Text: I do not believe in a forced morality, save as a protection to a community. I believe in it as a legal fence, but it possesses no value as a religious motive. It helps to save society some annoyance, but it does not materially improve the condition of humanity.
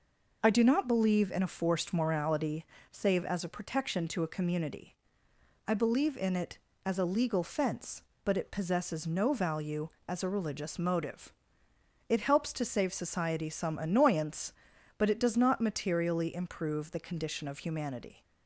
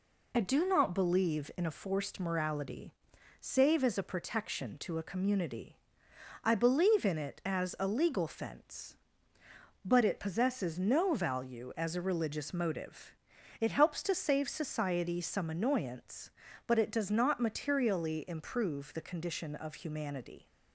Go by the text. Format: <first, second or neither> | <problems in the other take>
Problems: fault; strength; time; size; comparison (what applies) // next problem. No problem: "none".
neither | none